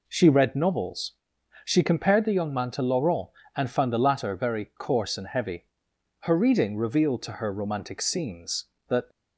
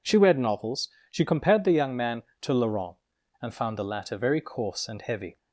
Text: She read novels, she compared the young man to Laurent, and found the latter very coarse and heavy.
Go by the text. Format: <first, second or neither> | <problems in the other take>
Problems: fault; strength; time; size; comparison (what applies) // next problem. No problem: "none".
second | goes on to say "Her reading revealed to her romantic scenes that"; strong; from 6.2 s on; 2.8 s long